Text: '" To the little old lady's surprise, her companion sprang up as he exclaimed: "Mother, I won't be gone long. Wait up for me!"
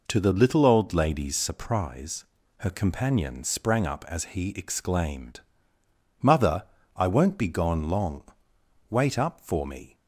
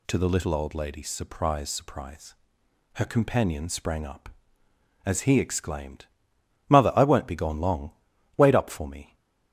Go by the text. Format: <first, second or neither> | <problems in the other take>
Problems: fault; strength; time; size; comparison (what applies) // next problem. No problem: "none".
first | says "surprise" twice; at 1.6 s